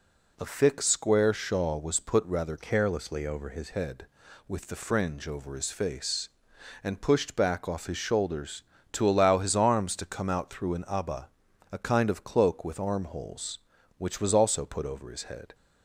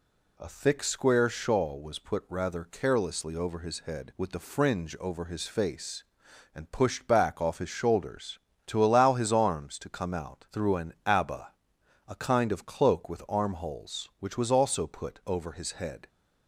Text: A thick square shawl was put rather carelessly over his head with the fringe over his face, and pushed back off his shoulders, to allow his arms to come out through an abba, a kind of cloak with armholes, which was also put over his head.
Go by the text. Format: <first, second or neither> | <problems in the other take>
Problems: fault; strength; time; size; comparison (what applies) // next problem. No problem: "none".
second | changes voice from "carelessly" to "his"; from 2.5 to 3.6 s; 1.1 s long